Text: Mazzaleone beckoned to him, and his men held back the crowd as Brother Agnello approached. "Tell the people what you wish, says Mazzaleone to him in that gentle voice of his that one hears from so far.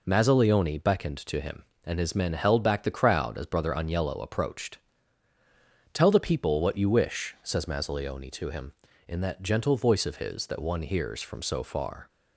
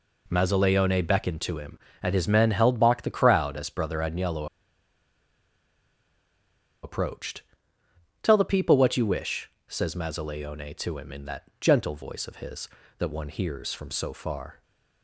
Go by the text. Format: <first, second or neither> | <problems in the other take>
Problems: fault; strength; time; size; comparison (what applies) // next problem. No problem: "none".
first | pauses between "Agnello" and "approached"; strong; at 4.4 s; 2.3 s long